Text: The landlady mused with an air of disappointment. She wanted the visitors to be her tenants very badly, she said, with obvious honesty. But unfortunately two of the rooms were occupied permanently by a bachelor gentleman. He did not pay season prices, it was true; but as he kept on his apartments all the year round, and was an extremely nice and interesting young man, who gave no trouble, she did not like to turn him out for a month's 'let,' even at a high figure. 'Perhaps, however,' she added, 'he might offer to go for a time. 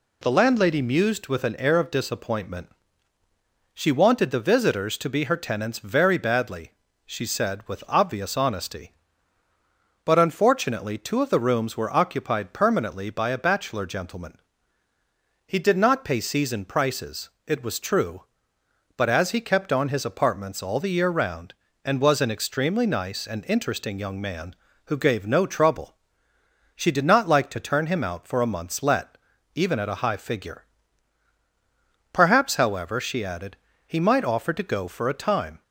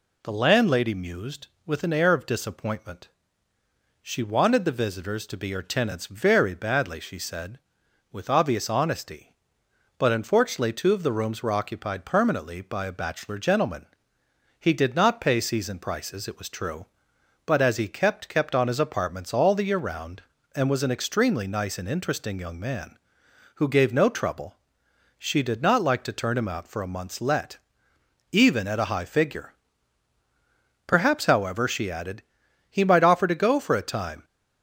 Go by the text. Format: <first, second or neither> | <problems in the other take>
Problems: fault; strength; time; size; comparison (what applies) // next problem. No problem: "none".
first | says "kept" twice; at 18.2 s